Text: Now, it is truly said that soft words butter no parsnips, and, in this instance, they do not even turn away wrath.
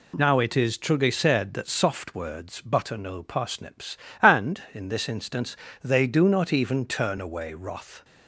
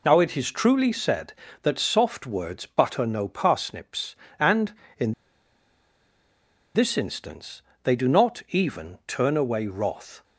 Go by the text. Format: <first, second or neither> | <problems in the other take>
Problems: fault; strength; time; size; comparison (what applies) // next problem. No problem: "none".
first | pauses between "in" and "this"; strong; at 5.1 s; 1.6 s long